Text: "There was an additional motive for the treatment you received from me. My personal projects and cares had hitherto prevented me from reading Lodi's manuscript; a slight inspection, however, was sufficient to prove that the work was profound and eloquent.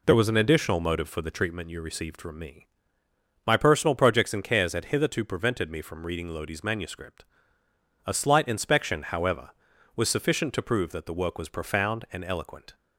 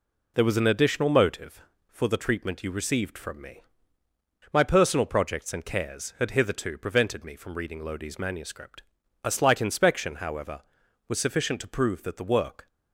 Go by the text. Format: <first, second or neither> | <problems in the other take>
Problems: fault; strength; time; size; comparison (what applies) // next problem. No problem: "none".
first | stops before "was profound and eloquent"; at 12.6 s